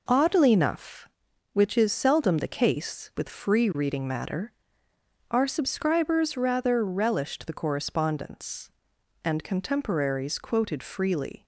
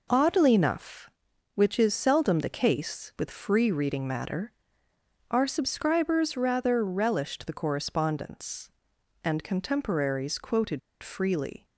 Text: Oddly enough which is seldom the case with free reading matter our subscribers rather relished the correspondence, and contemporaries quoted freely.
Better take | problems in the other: first | pauses between "matter" and "our"; noticeable; at 4.5 s; 0.78 s long; noticeable in the first // pauses between "quoted" and "freely"; slight; at 10.7 s; 0.22 s long

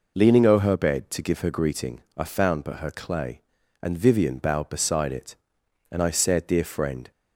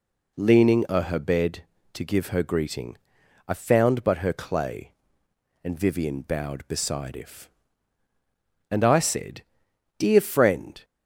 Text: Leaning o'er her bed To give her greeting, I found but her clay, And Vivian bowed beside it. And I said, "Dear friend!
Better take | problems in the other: first | says "if" for "it"; at 7.1 s

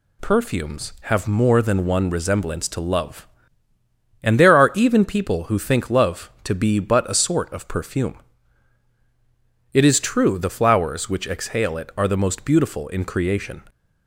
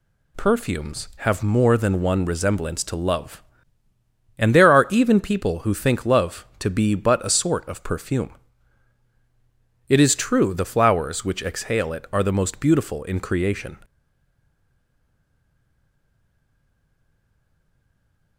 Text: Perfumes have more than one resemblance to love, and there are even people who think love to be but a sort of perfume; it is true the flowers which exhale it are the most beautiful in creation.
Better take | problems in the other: first | stays silent after the last word; strong; from 13.8 s on; 4.5 s long

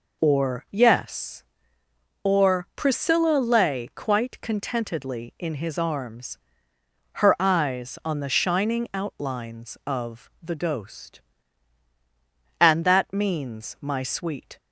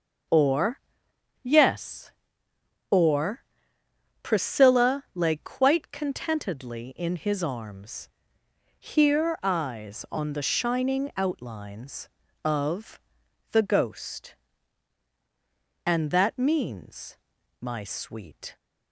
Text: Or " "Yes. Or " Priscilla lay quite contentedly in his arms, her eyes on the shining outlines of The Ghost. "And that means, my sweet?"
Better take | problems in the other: first | says "here" for "her"; at 8.7 s // pauses between "of" and "The"; noticeable; at 12.9 s; 0.52 s long

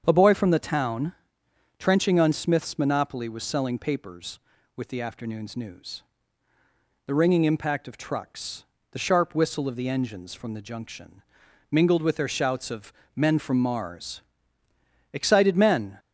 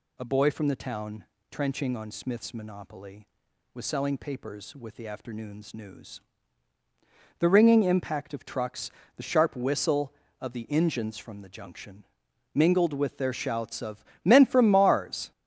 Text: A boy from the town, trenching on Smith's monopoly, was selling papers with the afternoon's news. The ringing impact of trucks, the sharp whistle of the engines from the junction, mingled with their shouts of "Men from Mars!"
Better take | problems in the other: second | starts louder than the rest; strong; until 1.0 s; 7.5 dB // pauses between "of" and "Men"; slight; at 12.9 s; 0.22 s long; slight in the second // goes on to say "Excited men"; noticeable; from 15.1 s on; 0.86 s long

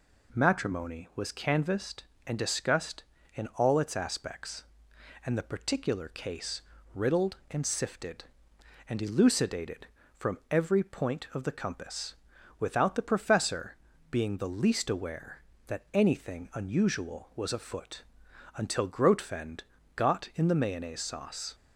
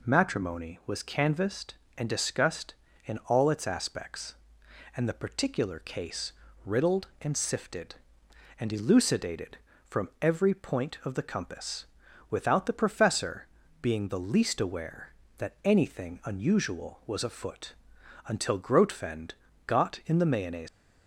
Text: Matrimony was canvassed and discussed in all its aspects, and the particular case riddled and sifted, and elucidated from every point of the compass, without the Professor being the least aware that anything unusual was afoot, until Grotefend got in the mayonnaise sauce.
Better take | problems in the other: first | pauses between "case" and "riddled"; slight; at 6.3 s; 0.34 s long; slight in the first // pauses between "Professor" and "being"; slight; at 13.4 s; 0.36 s long; slight in the first // pauses between "Grotefend" and "got"; slight; at 19.3 s; 0.34 s long; slight in the first // stops before "sauce"; at 20.6 s

